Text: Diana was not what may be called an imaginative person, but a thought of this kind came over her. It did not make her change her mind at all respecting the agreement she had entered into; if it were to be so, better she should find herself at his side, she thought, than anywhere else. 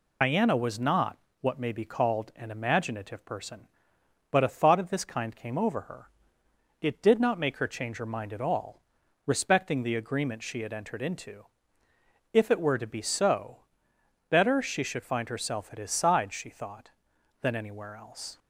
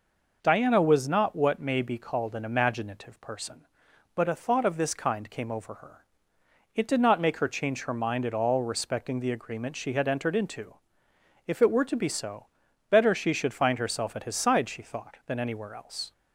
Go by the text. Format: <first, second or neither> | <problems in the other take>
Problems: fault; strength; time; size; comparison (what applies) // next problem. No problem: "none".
second | loses the start of "Diana"; at 0.2 s; 105 ms // pauses between "not" and "what"; slight; at 1.1 s; 0.22 s long // pauses between "all" and "respecting"; at 8.8 s; 0.44 s long